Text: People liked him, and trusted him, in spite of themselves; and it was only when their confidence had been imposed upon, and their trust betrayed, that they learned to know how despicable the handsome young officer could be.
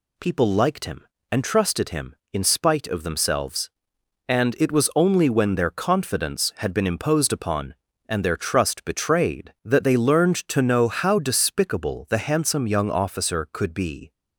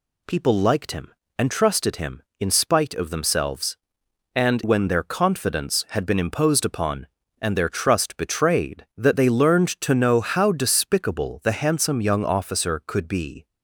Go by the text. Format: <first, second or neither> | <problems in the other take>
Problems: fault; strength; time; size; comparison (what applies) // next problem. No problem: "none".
first | skips "it was only"; at 4.6 s